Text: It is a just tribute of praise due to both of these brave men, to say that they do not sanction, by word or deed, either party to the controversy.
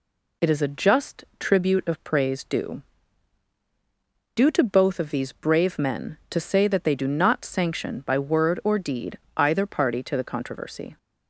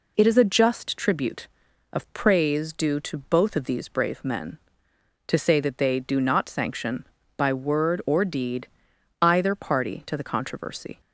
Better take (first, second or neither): second